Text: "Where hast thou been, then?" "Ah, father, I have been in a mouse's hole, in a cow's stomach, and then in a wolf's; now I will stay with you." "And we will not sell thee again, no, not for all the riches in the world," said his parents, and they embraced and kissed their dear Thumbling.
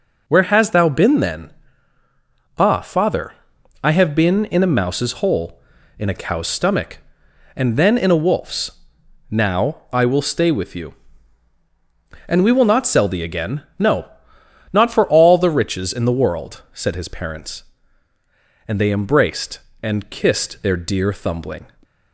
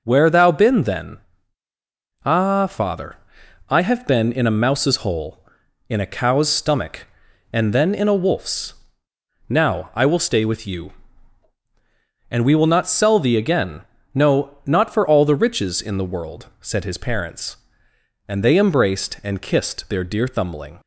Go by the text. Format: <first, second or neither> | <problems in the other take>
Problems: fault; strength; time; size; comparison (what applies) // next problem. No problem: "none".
first | skips "hast"; at 0.2 s